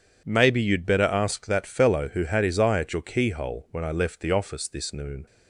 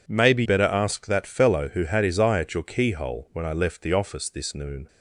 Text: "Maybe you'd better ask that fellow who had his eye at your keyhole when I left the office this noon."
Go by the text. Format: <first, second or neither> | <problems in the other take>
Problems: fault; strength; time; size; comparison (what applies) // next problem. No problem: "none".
first | skips "you'd"; at 0.4 s